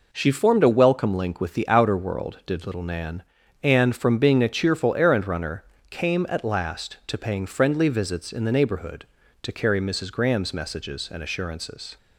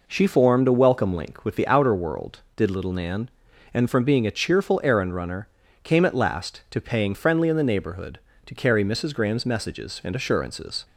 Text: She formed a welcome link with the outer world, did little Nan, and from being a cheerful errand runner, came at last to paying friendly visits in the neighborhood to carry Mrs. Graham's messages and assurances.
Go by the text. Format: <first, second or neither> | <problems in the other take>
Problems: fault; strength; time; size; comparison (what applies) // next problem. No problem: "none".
first | skips "visits"; at 7.4 s